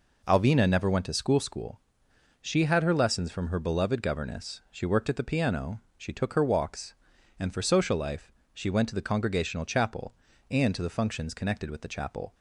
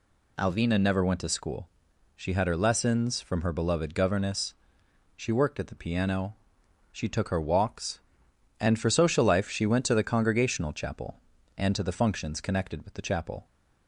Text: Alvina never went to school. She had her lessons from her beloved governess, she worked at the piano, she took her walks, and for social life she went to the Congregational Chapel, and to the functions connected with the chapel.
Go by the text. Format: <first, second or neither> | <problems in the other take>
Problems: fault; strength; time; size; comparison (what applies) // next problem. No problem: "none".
second | says "school" twice; at 1.4 s // pauses between "life" and "she"; slight; at 8.3 s; 0.20 s long